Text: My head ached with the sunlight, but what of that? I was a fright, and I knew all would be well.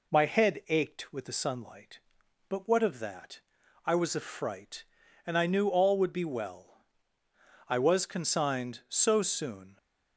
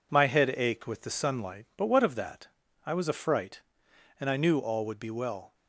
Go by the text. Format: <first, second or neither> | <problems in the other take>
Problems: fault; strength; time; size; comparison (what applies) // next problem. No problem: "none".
second | goes on to say "I was consigned so soon"; strong; from 7.6 s on; 2.1 s long